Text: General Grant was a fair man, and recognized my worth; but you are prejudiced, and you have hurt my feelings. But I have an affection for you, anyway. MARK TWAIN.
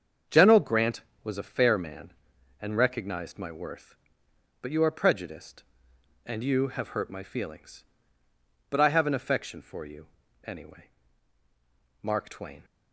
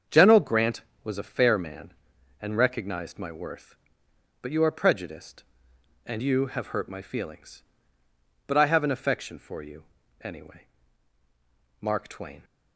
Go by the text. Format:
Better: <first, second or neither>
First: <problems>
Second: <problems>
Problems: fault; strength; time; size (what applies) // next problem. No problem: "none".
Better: neither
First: starts louder than the rest; strong; until 1.4 s; 7 dB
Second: starts louder than the rest; strong; until 1.3 s; 7 dB